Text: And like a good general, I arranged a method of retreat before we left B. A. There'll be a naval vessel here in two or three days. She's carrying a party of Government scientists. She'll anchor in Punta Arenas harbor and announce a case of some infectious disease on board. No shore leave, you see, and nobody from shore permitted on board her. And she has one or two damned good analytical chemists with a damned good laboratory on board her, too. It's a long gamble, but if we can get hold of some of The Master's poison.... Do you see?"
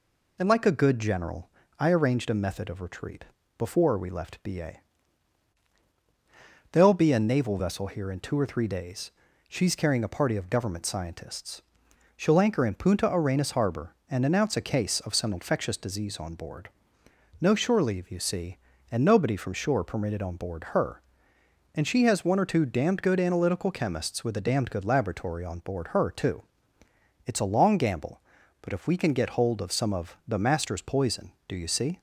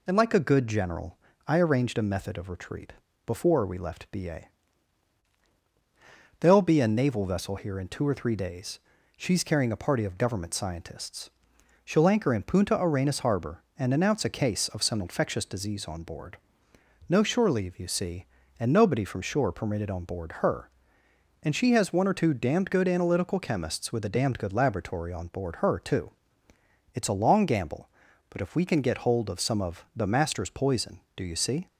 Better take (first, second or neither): neither